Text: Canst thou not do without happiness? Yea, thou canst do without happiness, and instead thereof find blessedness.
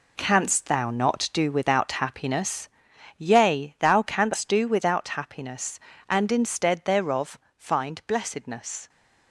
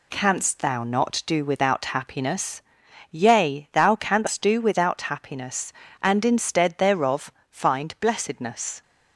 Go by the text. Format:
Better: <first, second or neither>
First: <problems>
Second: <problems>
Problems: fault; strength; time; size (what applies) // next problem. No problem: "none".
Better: second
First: gets quieter; strong; throughout; 8.5 dB // pauses between "thereof" and "find"; slight; at 7.3 s; 0.22 s long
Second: pauses between "thereof" and "find"; slight; at 7.2 s; 0.22 s long